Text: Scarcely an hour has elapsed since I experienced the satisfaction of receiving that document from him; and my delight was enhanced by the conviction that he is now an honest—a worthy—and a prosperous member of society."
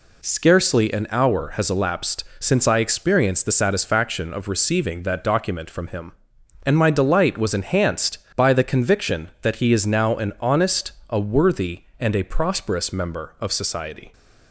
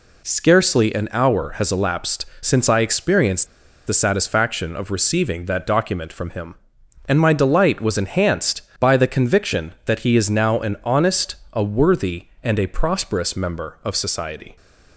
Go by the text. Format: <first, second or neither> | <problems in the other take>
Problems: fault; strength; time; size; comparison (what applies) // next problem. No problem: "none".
first | pauses between "elapsed" and "since"; slight; at 2.2 s; 0.16 s long; slight in the first // pauses between "experienced" and "the"; at 3.4 s; 0.40 s long